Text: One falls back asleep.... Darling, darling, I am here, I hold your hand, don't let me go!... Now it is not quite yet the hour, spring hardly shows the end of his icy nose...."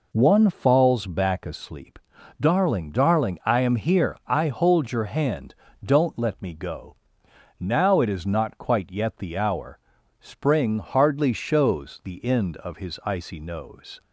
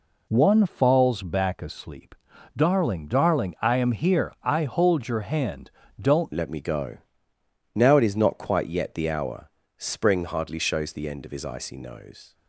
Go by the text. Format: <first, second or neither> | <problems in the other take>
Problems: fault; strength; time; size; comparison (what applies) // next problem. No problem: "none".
first | changes voice at "let"; from 6.3 s on; 6.0 s long